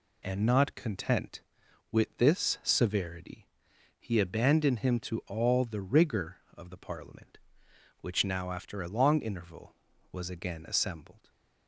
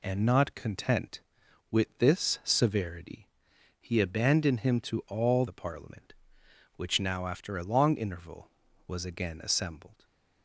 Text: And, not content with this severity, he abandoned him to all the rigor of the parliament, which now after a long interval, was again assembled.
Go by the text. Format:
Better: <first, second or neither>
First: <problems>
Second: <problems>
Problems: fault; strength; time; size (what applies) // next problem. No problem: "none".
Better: first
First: none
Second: skips "the rigor of"; at 5.4 s // stays silent after the last word; slight; from 9.9 s on; 0.5 s long